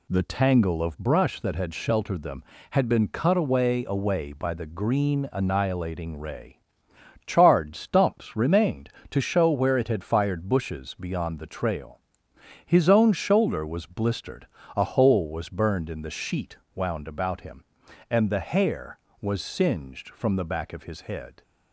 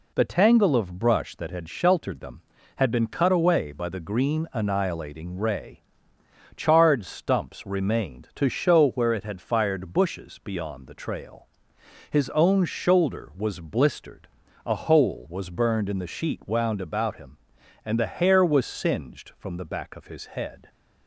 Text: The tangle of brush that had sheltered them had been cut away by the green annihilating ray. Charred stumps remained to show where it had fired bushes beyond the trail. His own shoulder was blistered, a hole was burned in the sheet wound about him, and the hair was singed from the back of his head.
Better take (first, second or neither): second